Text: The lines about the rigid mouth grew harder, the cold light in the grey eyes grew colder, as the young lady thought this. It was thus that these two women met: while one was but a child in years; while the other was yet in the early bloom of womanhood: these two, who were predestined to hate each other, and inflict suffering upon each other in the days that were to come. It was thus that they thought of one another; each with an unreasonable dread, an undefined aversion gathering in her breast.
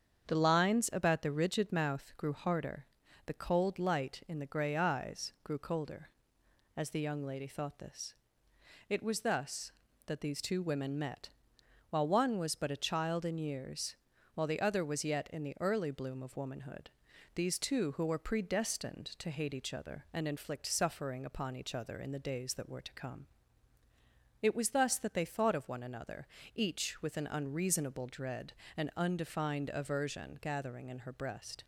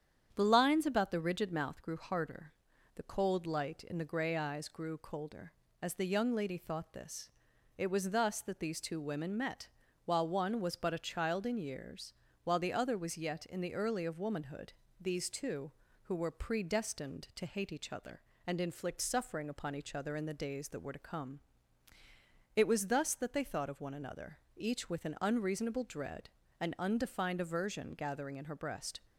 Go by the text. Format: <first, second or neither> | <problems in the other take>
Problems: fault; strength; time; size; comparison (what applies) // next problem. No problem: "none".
first | starts louder than the rest; strong; until 1.3 s; 8.5 dB; strong in the first // skips "bloom"; at 14.0 s